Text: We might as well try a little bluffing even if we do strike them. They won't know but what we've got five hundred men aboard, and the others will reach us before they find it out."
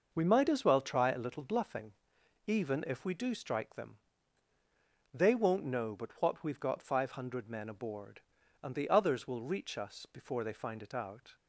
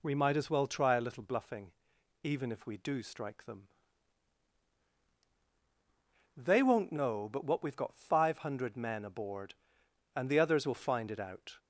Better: first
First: pauses between "bluffing" and "even"; noticeable; at 1.9 s; 0.52 s long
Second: pauses between "bluffing" and "even"; noticeable; at 1.7 s; 0.52 s long // skips "reach us before they"; at 10.7 s

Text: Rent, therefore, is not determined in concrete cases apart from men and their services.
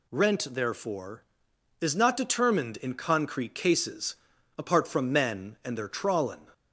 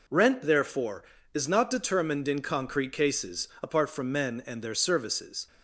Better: second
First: pauses between "cases" and "apart"; at 4.1 s; 0.42 s long // says "trawlin" for "services"; at 5.8 s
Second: none

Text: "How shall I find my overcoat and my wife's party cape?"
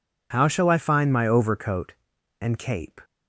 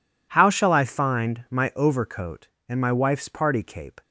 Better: second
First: skips "my wife's party"; at 2.5 s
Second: none

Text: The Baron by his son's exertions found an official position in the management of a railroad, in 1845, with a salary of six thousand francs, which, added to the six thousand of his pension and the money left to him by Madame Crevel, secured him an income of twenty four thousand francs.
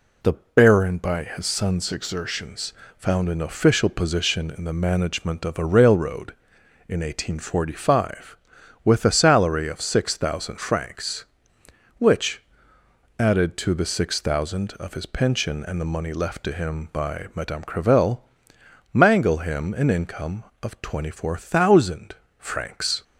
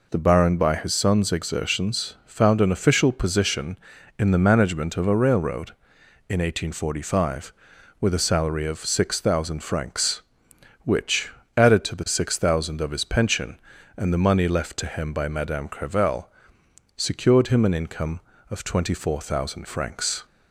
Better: second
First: pauses between "exertions" and "found"; slight; at 2.7 s; 0.26 s long // says "mangle" for "secured"; at 18.9 s // pauses between "thousand" and "francs"; slight; at 22.1 s; 0.24 s long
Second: none

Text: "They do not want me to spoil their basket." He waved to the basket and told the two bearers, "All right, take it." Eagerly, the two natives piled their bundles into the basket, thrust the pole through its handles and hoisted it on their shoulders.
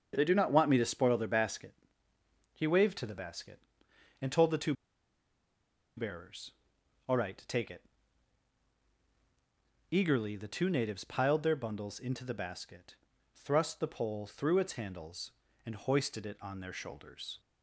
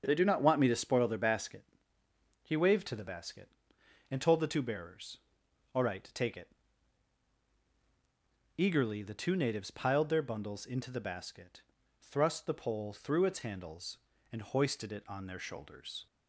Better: second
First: starts louder than the rest; until 1.1 s; 7 dB // pauses between "two" and "bearers"; at 4.7 s; 1.2 s long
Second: starts louder than the rest; until 1.0 s; 7 dB

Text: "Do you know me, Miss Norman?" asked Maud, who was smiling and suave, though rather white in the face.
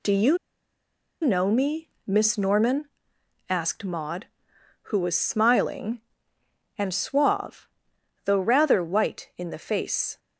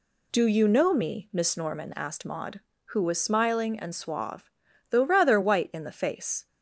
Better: second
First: pauses between "you" and "know"; noticeable; at 0.3 s; 0.85 s long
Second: none

